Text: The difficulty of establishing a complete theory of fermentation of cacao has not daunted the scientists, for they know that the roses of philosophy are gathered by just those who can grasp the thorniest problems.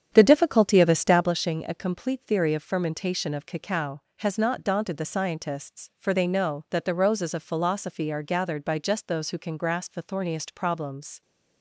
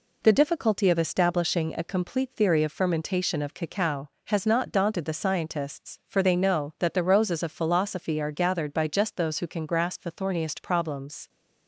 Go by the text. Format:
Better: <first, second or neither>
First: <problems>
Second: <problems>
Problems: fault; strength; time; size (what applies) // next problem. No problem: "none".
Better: second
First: starts louder than the rest; strong; until 1.4 s; 8.5 dB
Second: none